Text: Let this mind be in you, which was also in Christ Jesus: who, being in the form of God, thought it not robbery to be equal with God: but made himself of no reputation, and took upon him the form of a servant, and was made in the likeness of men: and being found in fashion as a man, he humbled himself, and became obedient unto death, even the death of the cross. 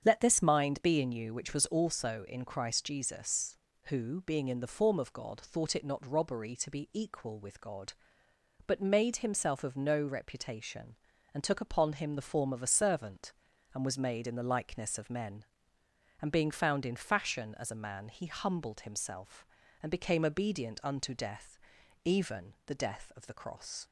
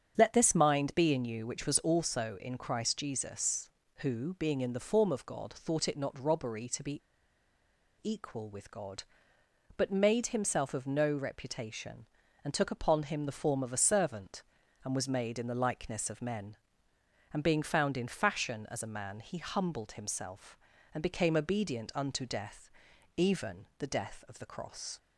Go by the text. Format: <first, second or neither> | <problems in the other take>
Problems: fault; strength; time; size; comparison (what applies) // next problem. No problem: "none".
first | starts louder than the rest; strong; until 1.1 s; 8 dB; strong in the first // pauses between "be" and "equal"; at 7.0 s; 1.0 s long